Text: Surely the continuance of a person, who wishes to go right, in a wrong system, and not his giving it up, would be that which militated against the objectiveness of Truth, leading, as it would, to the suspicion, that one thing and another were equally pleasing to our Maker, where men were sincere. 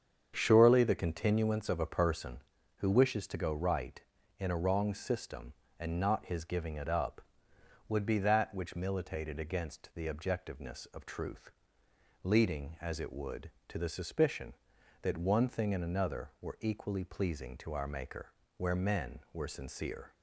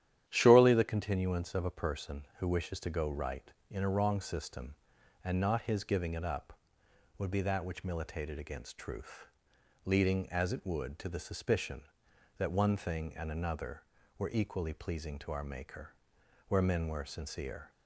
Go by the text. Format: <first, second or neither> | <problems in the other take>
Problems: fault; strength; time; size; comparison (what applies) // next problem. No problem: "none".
first | starts louder than the rest; strong; until 1.2 s; 11 dB; strong in the first // skips "the objectiveness of"; at 8.7 s